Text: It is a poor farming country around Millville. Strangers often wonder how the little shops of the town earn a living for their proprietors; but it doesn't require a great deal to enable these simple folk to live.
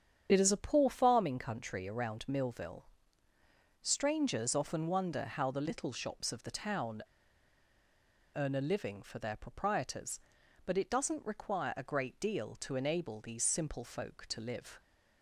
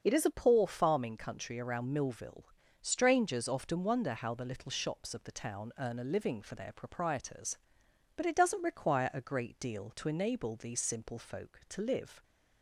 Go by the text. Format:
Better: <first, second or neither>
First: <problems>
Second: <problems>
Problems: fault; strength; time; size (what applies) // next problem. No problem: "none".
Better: second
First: starts louder than the rest; strong; until 1.3 s; 8 dB // pauses between "town" and "earn"; strong; at 7.0 s; 1.3 s long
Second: starts louder than the rest; until 1.0 s; 6.5 dB